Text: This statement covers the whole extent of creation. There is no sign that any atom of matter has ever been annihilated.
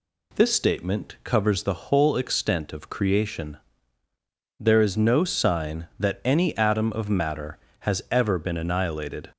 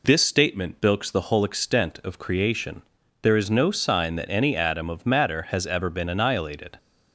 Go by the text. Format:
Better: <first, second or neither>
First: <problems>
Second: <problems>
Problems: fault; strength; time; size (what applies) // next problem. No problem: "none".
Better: first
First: none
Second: says "bilks" for "covers"; at 0.8 s